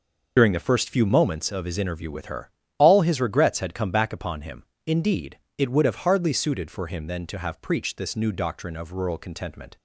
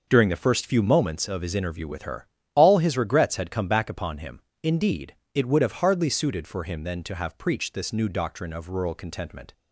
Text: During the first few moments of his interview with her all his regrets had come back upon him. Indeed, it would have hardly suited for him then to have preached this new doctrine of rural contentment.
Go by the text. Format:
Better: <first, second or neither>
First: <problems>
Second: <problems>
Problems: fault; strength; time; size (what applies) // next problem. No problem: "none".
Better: second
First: loses the start of "During"; at 0.3 s; 45 ms // pauses between "her" and "all"; slight; at 2.4 s; 0.28 s long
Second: pauses between "her" and "all"; slight; at 2.2 s; 0.28 s long